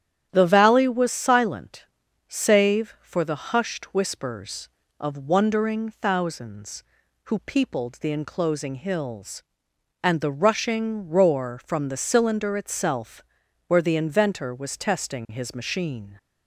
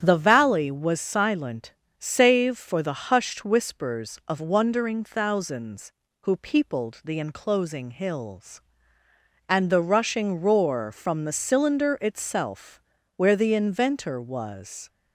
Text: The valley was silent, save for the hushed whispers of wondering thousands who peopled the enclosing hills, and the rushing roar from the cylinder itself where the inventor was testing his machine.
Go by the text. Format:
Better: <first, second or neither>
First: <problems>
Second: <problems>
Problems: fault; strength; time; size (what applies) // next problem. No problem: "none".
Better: first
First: starts louder than the rest; strong; until 1.3 s; 10 dB // pauses between "itself" and "where"; at 13.2 s; 0.42 s long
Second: starts louder than the rest; strong; until 1.0 s; 8.5 dB // pauses between "itself" and "where"; slight; at 12.8 s; 0.36 s long // stops before "testing his machine"; at 14.8 s